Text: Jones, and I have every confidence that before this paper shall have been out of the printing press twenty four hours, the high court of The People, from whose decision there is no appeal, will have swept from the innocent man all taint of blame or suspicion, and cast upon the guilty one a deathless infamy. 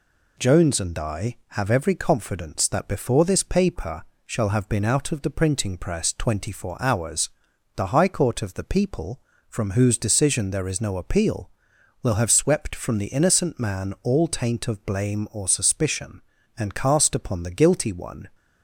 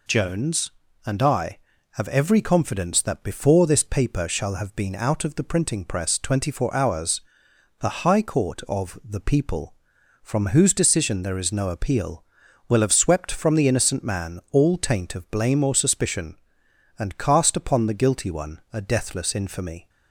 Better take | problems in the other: second | pauses between "paper" and "shall"; slight; at 4.0 s; 0.22 s long // stops before "a deathless infamy"; at 18.3 s

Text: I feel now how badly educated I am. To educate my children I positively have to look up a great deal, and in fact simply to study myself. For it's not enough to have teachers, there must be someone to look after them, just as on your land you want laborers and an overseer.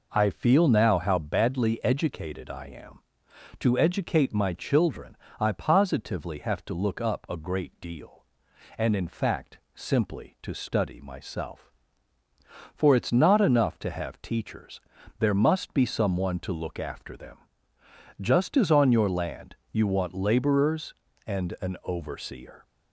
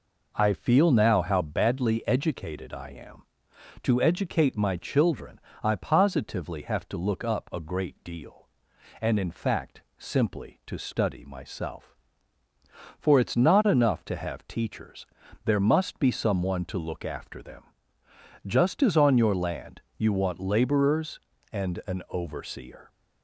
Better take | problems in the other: neither | pauses between "children" and "I"; slight; the same in both // pauses between "fact" and "simply"; slight; the same in both // pauses between "land" and "you"; slight; the same in both

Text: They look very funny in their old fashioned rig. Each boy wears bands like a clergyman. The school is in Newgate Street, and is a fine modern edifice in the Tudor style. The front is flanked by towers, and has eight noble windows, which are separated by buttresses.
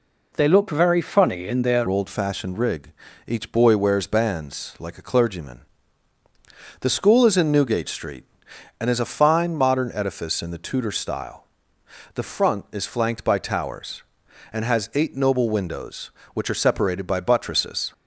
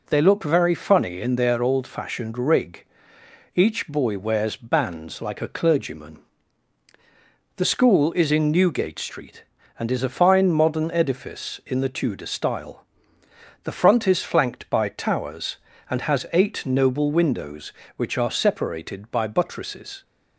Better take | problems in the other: second | changes voice at "old"; from 1.8 s on; 16.1 s long

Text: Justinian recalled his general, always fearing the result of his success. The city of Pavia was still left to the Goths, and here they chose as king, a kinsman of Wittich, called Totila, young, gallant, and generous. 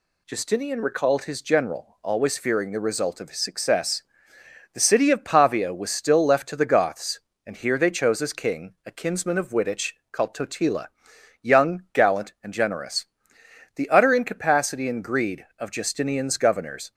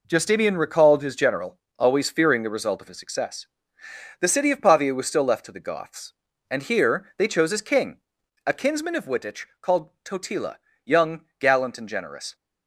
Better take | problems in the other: second | goes on to say "The utter incapacity and greed of Justinian's governors"; strong; from 13.7 s on; 3.1 s long

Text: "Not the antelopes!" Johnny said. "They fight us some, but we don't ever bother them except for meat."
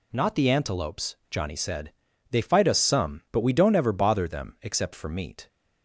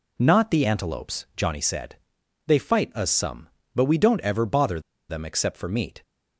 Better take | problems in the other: first | pauses between "bother" and "them"; slight; at 4.8 s; 0.28 s long

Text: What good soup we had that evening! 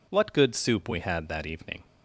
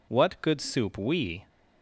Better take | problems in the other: first | stops before "had that evening"; at 1.4 s

